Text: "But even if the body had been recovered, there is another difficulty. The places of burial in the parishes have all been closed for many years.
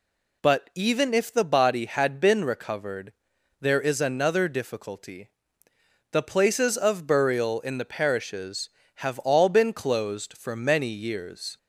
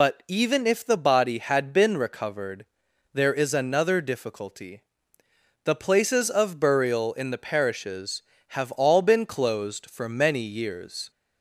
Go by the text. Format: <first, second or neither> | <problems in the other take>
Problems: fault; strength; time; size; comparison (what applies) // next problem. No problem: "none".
first | loses the start of "But"; at 0.0 s; 60 ms